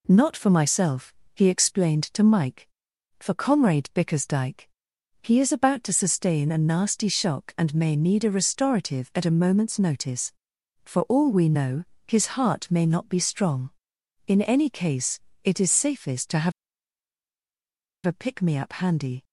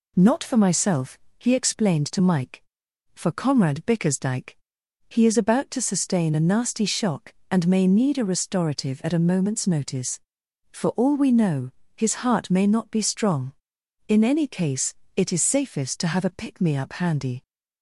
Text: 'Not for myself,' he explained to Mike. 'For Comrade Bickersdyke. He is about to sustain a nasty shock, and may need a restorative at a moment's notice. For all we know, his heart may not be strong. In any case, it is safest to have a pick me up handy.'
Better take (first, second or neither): second